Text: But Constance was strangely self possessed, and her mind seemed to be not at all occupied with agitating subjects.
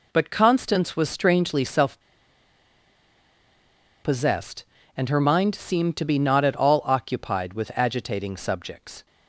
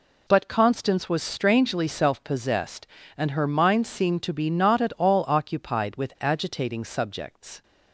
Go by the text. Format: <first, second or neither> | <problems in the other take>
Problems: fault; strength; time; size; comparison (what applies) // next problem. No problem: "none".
second | pauses between "self" and "possessed"; strong; at 2.0 s; 2.0 s long